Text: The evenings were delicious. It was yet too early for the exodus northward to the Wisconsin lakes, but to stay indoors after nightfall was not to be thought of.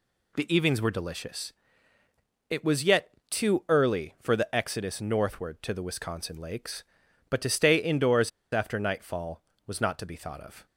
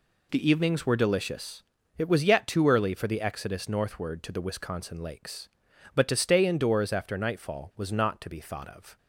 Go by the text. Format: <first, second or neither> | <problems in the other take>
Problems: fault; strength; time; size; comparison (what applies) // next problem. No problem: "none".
second | pauses between "yet" and "too"; slight; at 3.0 s; 0.20 s long // pauses between "indoors" and "after"; slight; at 8.3 s; 0.23 s long